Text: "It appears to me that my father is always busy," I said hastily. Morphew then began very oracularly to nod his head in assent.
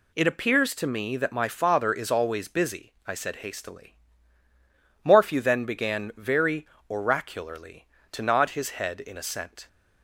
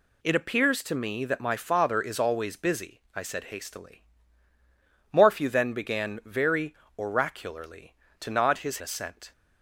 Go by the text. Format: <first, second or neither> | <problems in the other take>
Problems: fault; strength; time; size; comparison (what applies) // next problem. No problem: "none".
first | pauses between "very" and "oracularly"; slight; at 6.7 s; 0.22 s long; slight in the first // skips "head in"; at 8.8 s